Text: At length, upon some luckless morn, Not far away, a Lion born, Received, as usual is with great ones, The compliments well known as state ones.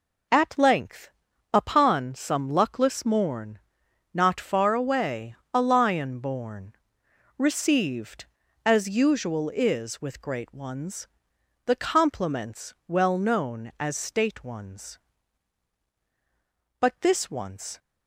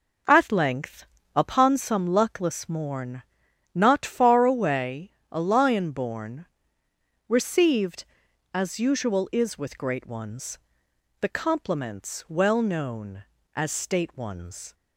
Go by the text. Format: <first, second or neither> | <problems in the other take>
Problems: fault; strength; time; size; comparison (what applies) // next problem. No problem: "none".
second | goes on to say "But this once"; noticeable; from 16.8 s on; 0.98 s long